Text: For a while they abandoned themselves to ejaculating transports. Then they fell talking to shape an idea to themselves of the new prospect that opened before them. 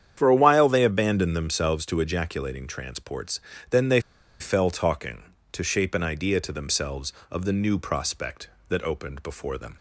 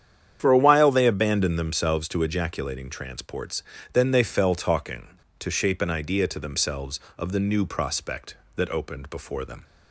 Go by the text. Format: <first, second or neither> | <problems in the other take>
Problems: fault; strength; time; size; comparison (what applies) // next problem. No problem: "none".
second | starts louder than the rest; strong; until 1.1 s; 9 dB; strong in the second // pauses between "they" and "fell"; at 4.0 s; 0.39 s long